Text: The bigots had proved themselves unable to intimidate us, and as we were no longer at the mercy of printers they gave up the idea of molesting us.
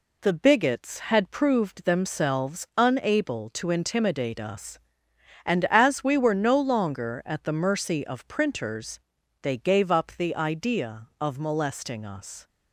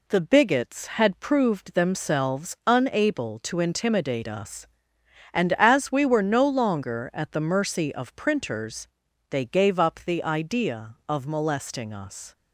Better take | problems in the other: neither | pauses between "printers" and "they"; the same in both

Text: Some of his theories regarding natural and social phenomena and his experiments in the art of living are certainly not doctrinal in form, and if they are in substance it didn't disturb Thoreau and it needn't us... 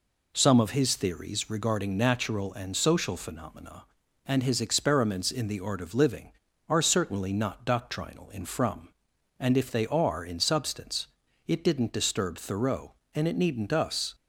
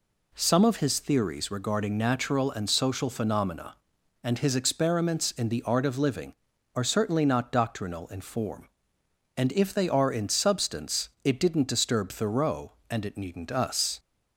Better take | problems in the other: second | says "from" for "form"; at 8.4 s // pauses between "substance" and "it"; at 11.0 s; 0.40 s long

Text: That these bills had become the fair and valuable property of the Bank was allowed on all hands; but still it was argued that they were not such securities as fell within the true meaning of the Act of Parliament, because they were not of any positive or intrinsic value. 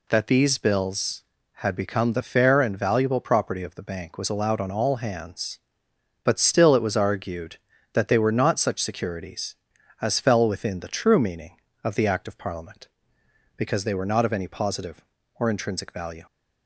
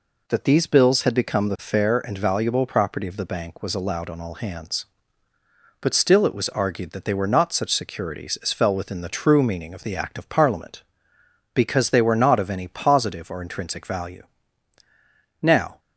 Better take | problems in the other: first | goes on to say "Now"; slight; from 15.4 s on; 0.38 s long

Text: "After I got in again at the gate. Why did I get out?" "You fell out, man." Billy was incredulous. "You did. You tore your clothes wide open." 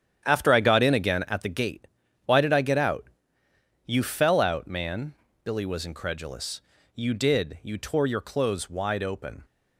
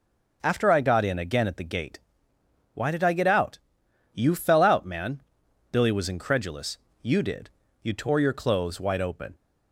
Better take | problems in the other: second | gets quieter; strong; throughout; 11 dB

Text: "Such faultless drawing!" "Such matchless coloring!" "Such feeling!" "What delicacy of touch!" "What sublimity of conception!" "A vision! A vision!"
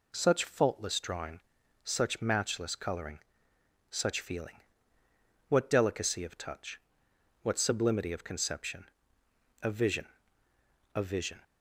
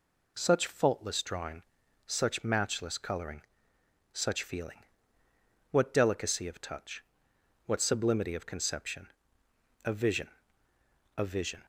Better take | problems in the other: neither | none

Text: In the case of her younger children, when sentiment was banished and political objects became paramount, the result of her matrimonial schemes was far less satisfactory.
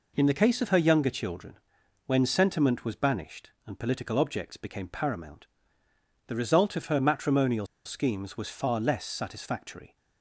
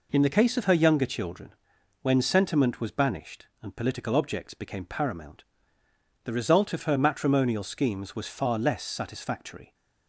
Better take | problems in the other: second | pauses between "matrimonial" and "schemes"; slight; at 7.6 s; 0.18 s long

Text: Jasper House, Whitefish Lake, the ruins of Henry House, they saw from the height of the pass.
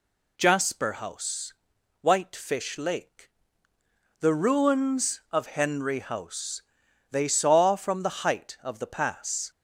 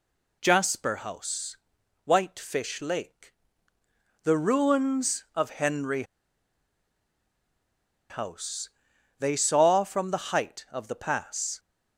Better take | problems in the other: first | pauses between "Henry" and "House"; strong; at 6.0 s; 2.0 s long

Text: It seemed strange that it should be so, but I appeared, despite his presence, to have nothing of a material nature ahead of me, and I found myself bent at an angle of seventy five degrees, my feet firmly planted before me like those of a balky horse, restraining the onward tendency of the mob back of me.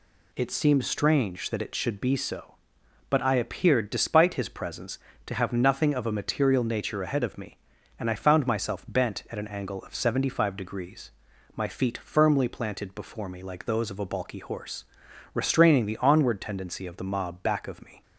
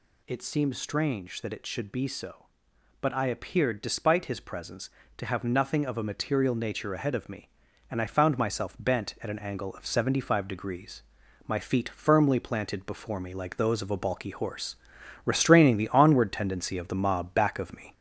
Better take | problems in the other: first | gets louder; slight; throughout; 3.5 dB

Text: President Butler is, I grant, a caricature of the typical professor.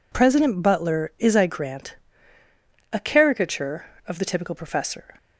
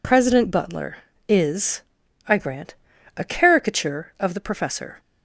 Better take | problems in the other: first | skips "typical"; at 4.3 s

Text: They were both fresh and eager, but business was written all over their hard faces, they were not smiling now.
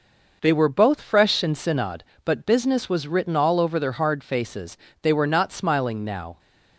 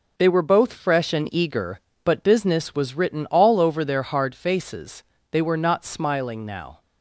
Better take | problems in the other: second | says "synod" for "eager"; at 1.5 s

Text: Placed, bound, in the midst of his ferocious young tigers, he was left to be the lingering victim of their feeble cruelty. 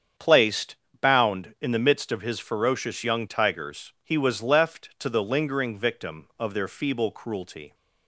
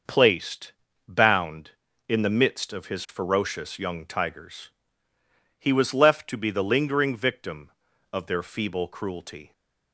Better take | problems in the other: second | starts louder than the rest; strong; until 1.4 s; 8 dB; noticeable in the second // skips "be"; at 5.0 s

